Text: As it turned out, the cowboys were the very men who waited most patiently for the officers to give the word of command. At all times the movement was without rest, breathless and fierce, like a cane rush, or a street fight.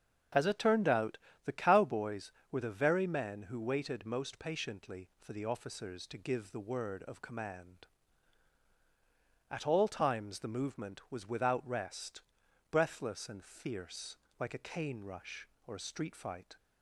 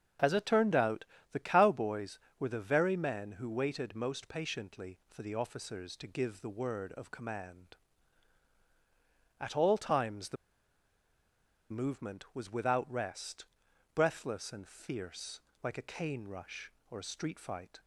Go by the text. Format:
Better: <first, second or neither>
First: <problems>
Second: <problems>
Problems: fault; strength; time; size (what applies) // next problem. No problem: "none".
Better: first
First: starts louder than the rest; until 1.6 s; 7 dB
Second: starts louder than the rest; until 1.4 s; 7 dB // pauses between "the" and "movement"; strong; at 10.3 s; 1.3 s long